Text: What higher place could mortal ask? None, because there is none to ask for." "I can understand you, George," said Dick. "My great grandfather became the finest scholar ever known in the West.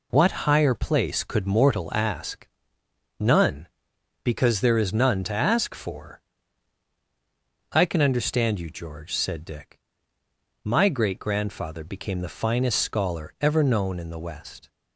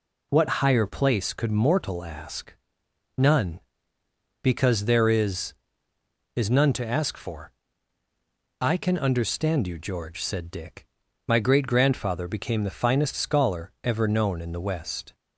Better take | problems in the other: first | says "is" twice; at 6.3 s

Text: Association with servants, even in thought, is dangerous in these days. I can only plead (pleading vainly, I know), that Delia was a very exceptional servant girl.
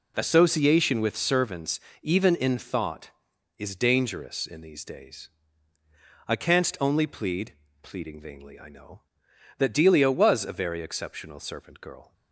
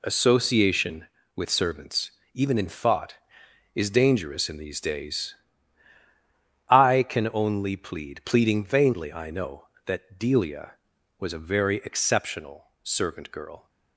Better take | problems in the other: second | says "canst" for "can"; at 6.3 s

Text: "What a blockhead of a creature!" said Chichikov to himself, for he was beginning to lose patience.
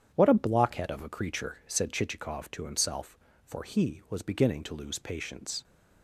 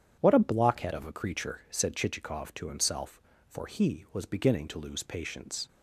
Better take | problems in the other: neither | starts louder than the rest; strong; the same in both

